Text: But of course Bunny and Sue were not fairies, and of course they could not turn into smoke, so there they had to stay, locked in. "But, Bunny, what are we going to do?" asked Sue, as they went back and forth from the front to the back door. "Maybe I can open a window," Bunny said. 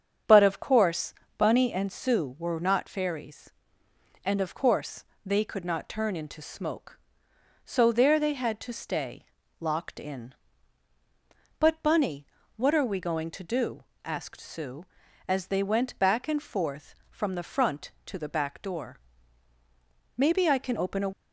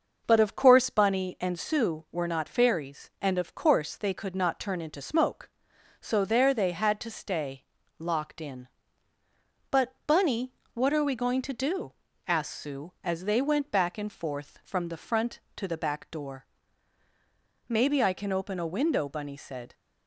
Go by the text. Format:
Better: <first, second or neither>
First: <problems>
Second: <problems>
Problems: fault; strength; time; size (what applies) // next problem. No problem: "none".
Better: second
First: starts louder than the rest; strong; until 1.5 s; 7.5 dB // pauses between "course" and "Bunny"; slight; at 1.1 s; 0.24 s long // pauses between "course" and "they"; slight; at 5.0 s; 0.20 s long // stops before "window Bunny said"; at 21.1 s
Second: starts louder than the rest; noticeable; until 1.2 s; 6 dB